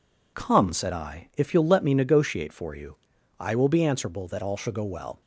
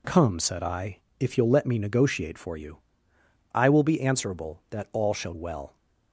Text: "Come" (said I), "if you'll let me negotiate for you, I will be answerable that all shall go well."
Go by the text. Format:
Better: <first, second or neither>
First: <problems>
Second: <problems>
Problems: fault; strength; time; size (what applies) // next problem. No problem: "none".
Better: first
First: none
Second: skips "go"; at 5.3 s